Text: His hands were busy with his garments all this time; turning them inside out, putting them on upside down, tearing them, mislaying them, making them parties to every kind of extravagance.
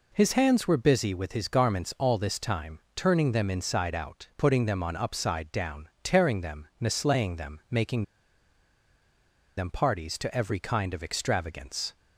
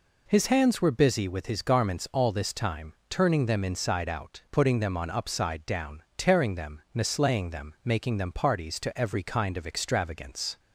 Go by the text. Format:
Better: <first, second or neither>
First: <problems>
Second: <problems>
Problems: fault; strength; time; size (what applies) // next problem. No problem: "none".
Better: second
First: pauses between "making" and "them"; strong; at 8.0 s; 1.5 s long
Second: none